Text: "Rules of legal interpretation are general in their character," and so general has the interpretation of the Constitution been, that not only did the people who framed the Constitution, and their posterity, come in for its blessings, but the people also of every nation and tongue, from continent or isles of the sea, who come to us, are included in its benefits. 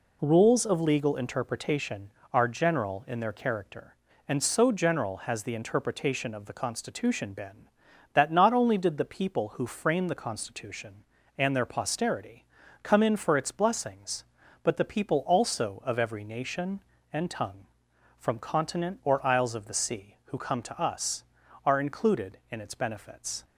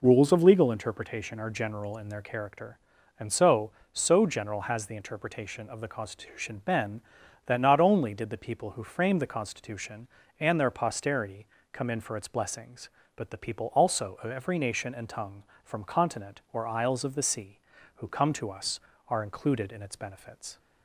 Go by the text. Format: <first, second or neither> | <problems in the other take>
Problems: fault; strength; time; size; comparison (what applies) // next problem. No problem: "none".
first | says "so" twice; at 3.9 s